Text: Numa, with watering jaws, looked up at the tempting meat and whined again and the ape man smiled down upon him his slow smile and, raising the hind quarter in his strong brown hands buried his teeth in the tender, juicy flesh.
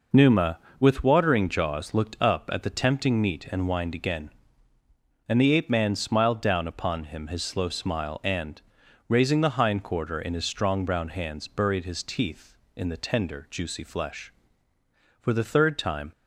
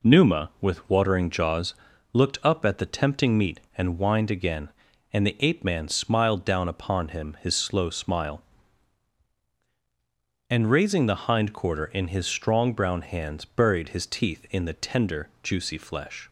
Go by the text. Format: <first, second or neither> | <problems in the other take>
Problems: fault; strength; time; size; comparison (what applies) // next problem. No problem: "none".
second | goes on to say "For the third time"; noticeable; from 15.2 s on; 0.88 s long